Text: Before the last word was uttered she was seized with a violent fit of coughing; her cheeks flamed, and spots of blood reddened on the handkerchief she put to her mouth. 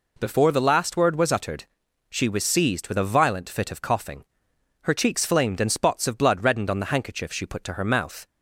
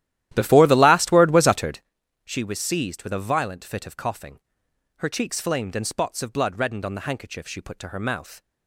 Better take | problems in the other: first | starts louder than the rest; strong; until 1.8 s; 13 dB // pauses between "uttered" and "she"; at 1.8 s; 0.44 s long; also in the first

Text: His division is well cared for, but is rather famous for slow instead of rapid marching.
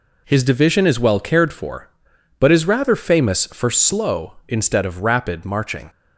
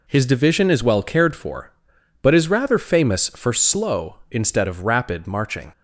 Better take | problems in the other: neither | none

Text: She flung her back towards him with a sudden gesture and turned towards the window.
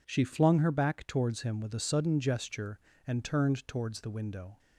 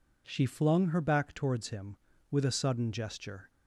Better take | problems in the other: first | stops before "and turned towards the window"; at 3.4 s

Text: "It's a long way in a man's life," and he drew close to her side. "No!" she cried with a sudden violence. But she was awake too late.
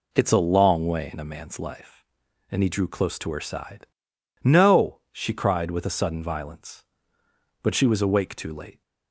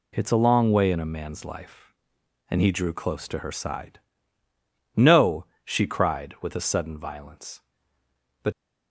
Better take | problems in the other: first | stops before "she was awake too late"; at 8.5 s

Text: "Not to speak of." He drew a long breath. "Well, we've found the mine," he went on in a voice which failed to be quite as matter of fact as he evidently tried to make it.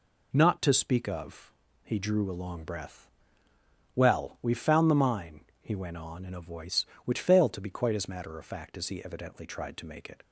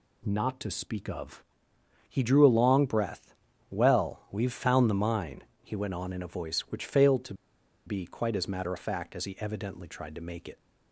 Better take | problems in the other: first | pauses between "to" and "be"; noticeable; at 7.3 s; 0.52 s long

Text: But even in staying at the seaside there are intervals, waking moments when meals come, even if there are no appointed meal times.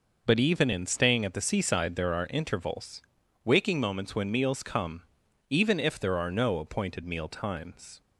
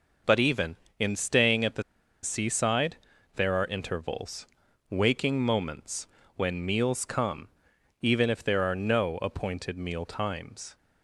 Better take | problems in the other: first | pauses between "the" and "seaside"; at 1.8 s; 0.41 s long // pauses between "seaside" and "there"; at 2.9 s; 0.38 s long // pauses between "moments" and "when"; slight; at 6.0 s; 0.30 s long

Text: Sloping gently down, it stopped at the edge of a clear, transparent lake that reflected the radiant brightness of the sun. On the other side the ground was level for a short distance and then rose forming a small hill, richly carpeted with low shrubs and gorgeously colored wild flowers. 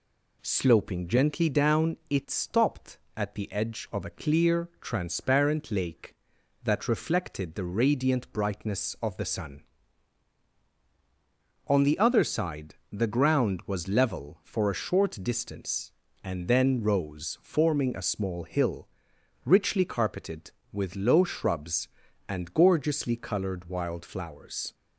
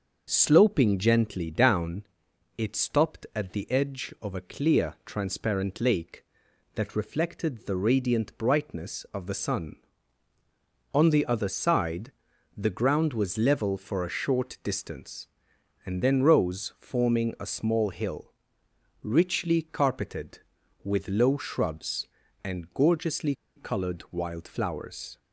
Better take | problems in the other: first | starts louder than the rest; noticeable; until 1.3 s; 6 dB // pauses between "side" and "the"; at 12.1 s; 0.44 s long; slight in the first // pauses between "gorgeously" and "colored"; slight; at 23.3 s; 0.23 s long

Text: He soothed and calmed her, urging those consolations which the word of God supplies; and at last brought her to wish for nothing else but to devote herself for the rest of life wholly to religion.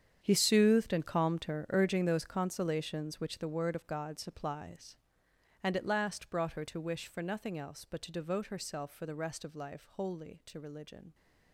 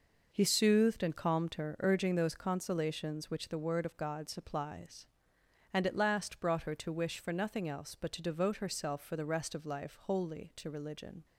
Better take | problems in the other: second | gets quieter; strong; throughout; 15.5 dB

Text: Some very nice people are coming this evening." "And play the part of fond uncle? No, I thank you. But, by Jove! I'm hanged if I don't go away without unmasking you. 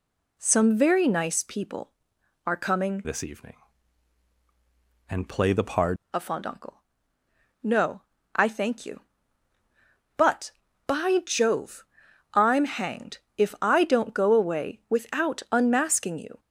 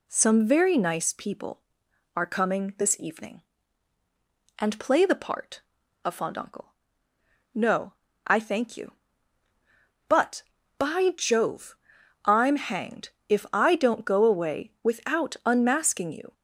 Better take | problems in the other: second | changes voice from "this" to "part"; from 3.0 to 5.9 s; 2.9 s long // pauses between "hanged" and "if"; slight; at 13.1 s; 0.18 s long; slight in the second

